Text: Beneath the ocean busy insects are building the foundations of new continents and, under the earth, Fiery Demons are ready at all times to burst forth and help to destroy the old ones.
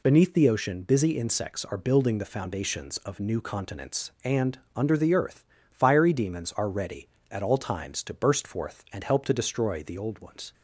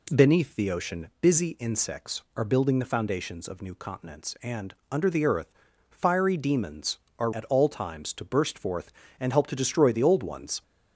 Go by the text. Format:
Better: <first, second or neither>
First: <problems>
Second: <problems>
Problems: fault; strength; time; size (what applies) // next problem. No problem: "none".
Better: first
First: none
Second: skips "ready"; at 7.3 s